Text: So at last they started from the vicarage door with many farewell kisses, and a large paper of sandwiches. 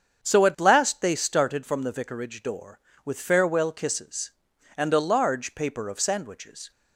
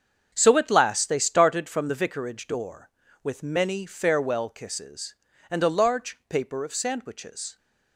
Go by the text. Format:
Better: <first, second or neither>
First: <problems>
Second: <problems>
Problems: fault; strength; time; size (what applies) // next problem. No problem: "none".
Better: second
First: starts louder than the rest; strong; until 1.2 s; 7 dB // skips "many"; at 3.2 s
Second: starts louder than the rest; strong; until 1.3 s; 7 dB